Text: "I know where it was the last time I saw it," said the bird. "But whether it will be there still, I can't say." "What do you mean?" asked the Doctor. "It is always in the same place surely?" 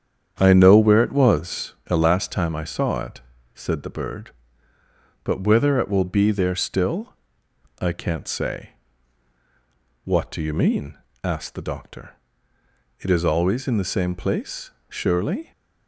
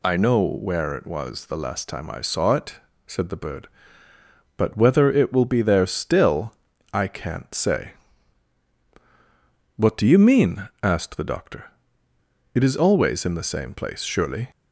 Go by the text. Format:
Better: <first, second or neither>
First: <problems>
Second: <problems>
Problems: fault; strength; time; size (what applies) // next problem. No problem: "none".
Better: second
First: starts louder than the rest; strong; until 1.9 s; 8.5 dB // pauses between "place" and "surely"; slight; at 14.7 s; 0.18 s long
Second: none